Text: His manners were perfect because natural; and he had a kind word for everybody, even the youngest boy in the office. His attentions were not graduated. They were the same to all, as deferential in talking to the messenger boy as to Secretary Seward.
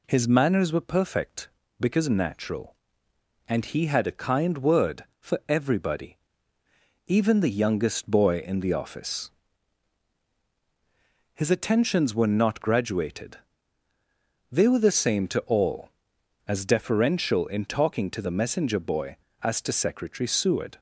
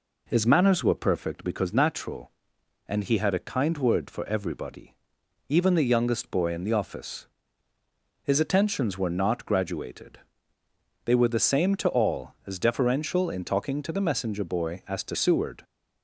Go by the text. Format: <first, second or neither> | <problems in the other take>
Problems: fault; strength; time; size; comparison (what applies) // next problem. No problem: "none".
first | skips "Secretary"; at 15.1 s